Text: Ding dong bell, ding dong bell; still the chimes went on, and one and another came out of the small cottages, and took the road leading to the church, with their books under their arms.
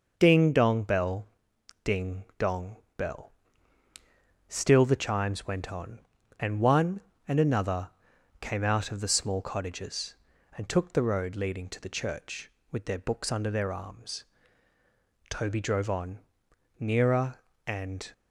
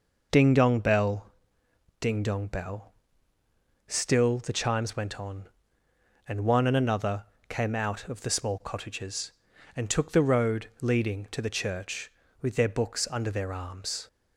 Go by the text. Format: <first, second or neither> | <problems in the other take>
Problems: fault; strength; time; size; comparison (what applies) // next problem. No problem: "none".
second | pauses between "dong" and "bell"; slight; at 2.7 s; 0.18 s long // pauses between "another" and "came"; noticeable; at 7.8 s; 0.50 s long; slight in the second // goes on to say "Toby drove on nearer and"; strong; from 15.3 s on; 2.8 s long